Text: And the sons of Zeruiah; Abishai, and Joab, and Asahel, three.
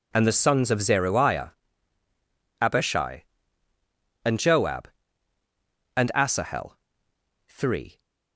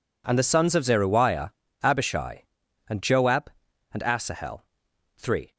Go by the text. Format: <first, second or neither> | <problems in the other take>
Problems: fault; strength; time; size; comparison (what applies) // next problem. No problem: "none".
neither | none